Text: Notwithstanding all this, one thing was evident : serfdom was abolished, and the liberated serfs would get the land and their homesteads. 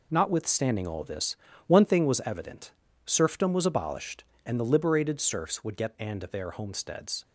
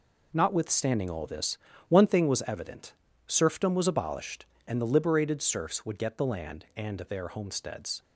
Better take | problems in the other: second | skips "the land"; at 5.9 s

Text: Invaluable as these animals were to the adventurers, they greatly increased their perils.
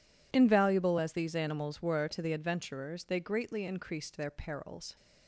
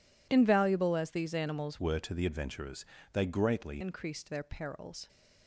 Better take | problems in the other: first | changes voice from "were" to "greatly"; from 1.7 to 3.8 s; 2.1 s long

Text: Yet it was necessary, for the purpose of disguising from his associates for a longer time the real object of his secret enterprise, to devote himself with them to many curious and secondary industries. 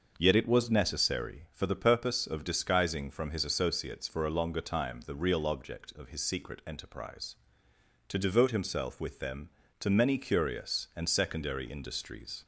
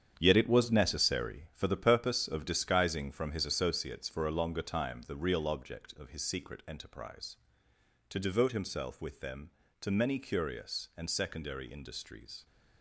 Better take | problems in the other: first | gets quieter; strong; throughout; 9.5 dB // starts louder than the rest; strong; until 1.1 s; 8.5 dB; also in the first

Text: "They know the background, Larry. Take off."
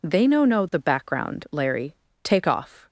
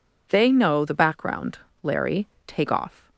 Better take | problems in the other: second | says "know" twice; at 0.4 s

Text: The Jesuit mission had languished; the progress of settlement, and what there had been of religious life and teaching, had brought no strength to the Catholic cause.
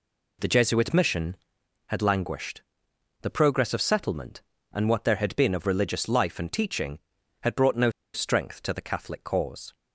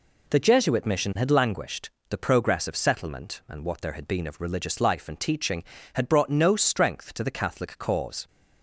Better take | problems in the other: second | pauses between "no" and "strength"; slight; at 7.8 s; 0.24 s long

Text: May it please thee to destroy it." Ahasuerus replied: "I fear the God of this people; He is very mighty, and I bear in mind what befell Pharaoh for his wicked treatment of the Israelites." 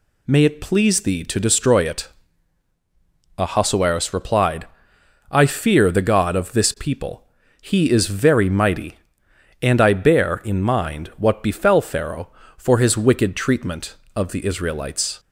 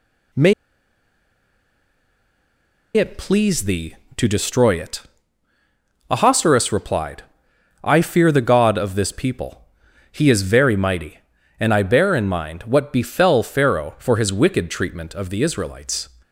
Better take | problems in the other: first | pauses between "May" and "it"; strong; at 0.5 s; 2.4 s long

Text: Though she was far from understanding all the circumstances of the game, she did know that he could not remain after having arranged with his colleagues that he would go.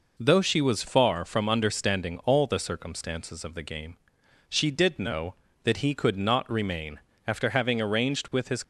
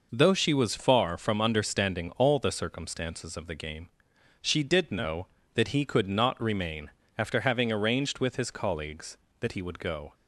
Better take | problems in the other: second | pauses between "remain" and "after"; slight; at 6.9 s; 0.28 s long; slight in the second // stops before "colleagues that he would go"; at 8.6 s

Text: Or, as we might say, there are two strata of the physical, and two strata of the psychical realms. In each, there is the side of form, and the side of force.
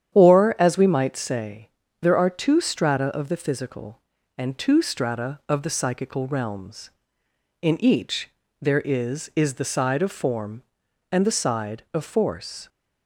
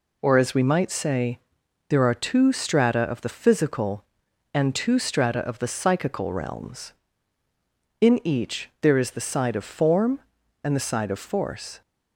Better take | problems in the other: second | starts louder than the rest; strong; until 1.1 s; 9.5 dB // says "is" twice; at 9.3 s

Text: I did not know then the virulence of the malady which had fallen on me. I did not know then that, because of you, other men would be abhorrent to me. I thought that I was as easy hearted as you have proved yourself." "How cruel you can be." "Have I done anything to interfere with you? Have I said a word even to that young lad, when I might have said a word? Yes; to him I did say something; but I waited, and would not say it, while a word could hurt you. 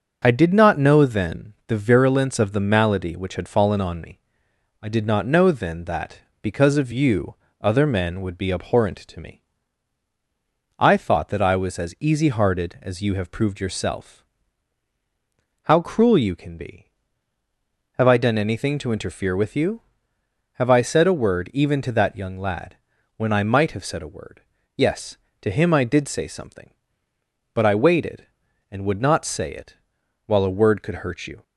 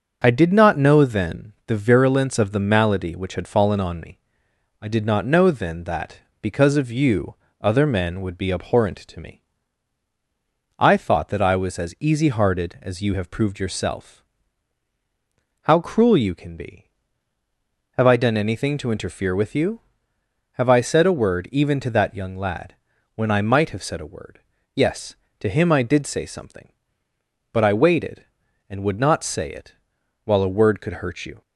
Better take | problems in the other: neither | starts louder than the rest; the same in both

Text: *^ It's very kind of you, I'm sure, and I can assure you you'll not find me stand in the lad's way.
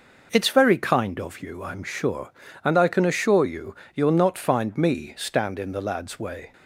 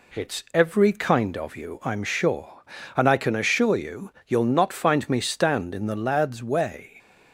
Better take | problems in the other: first | says "every" for "very"; at 0.5 s // pauses between "you" and "you'll"; slight; at 4.1 s; 0.18 s long; slight in the first

